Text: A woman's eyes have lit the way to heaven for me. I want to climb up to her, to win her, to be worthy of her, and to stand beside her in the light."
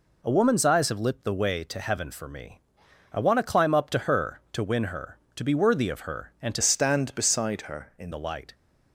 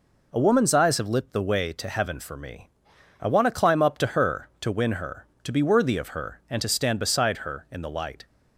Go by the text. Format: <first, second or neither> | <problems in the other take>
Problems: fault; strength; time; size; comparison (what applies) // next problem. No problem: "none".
second | changes voice from "stand" to "in"; from 6.6 to 8.1 s; 1.5 s long